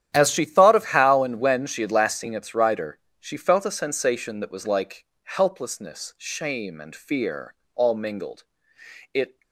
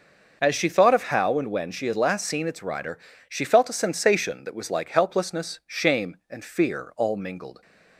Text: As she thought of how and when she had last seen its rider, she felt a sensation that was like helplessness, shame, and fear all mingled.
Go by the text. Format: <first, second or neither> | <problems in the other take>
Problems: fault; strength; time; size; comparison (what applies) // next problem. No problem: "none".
second | starts louder than the rest; strong; until 1.1 s; 10.5 dB // pauses between "like" and "helplessness"; slight; at 5.0 s; 0.18 s long // pauses between "fear" and "all"; slight; at 7.5 s; 0.20 s long // goes on to say "It"; slight; from 9.1 s on; 0.28 s long